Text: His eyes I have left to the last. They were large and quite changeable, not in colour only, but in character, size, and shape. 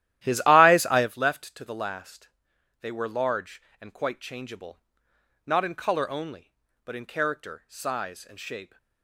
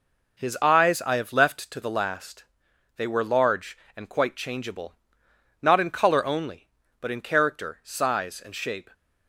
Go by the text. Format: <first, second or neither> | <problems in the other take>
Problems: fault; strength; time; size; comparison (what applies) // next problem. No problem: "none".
second | starts louder than the rest; strong; until 1.1 s; 13 dB